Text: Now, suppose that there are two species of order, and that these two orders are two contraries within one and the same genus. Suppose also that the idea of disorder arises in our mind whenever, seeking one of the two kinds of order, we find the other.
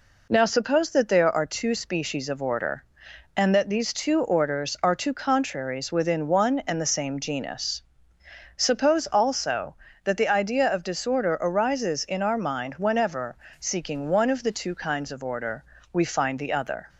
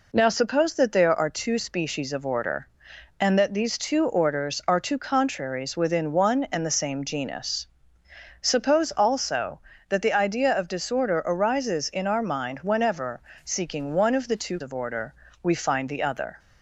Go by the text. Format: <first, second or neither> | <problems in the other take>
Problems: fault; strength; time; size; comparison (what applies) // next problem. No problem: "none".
first | skips "kinds"; at 14.6 s